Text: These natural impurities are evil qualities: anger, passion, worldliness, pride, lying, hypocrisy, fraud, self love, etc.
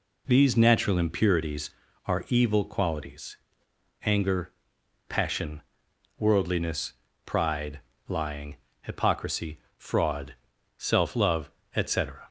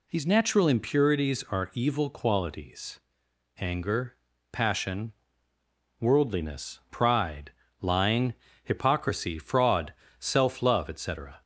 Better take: neither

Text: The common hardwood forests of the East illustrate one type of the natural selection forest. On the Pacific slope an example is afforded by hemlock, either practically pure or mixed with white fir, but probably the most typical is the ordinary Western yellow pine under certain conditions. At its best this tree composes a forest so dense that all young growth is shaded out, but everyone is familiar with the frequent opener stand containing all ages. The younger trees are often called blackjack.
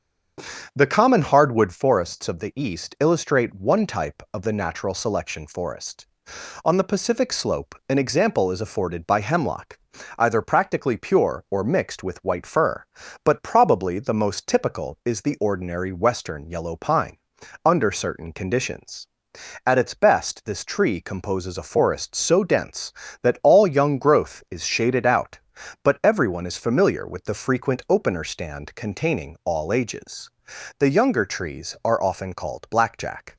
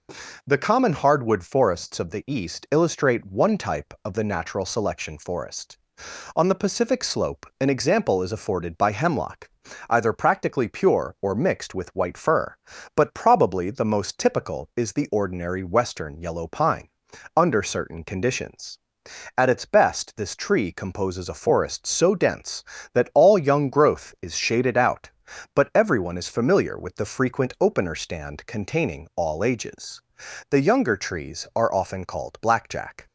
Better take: second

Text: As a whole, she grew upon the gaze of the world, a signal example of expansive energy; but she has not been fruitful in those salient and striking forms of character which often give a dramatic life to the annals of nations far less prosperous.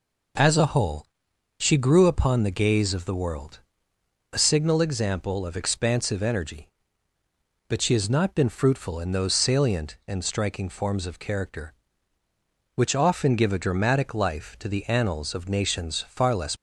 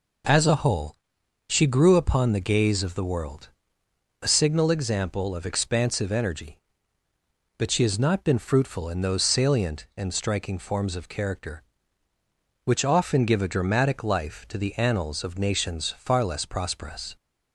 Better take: second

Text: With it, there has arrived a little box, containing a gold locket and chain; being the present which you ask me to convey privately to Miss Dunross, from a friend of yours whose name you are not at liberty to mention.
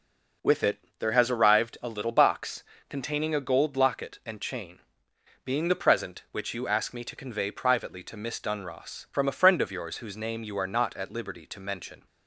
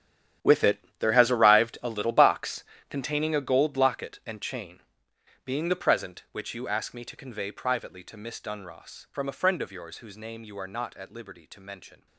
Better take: first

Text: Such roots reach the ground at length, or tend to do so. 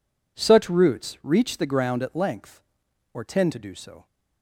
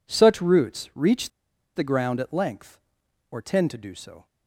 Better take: first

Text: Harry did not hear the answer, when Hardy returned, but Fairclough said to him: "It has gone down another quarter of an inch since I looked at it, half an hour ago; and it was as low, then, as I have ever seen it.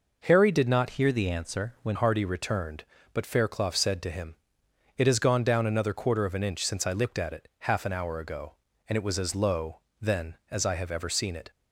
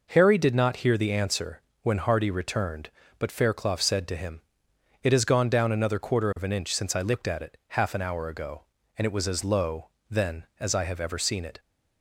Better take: second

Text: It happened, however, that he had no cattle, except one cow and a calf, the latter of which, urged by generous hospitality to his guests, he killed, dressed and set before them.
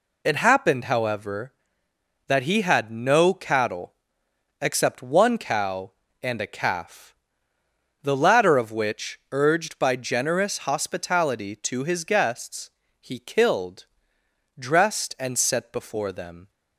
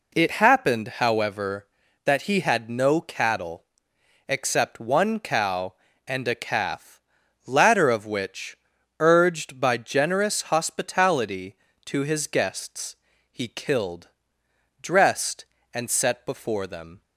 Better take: first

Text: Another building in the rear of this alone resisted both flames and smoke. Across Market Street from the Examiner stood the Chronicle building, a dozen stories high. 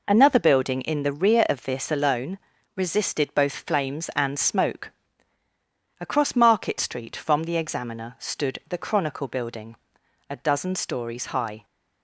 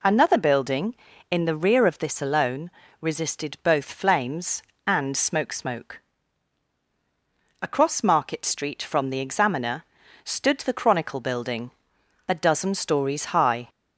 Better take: first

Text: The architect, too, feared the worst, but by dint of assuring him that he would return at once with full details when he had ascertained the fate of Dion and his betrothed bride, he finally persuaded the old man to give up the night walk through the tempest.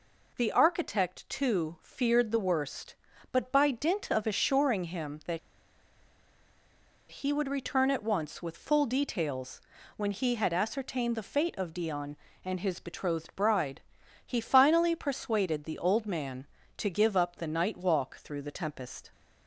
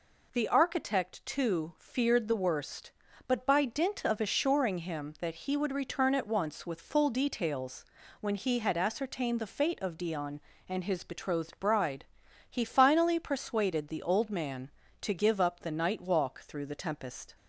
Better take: second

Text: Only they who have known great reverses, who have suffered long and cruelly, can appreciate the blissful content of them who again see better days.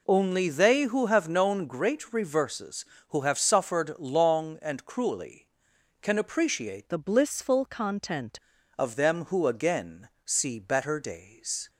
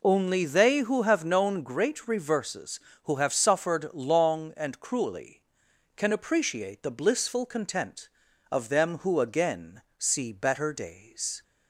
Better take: second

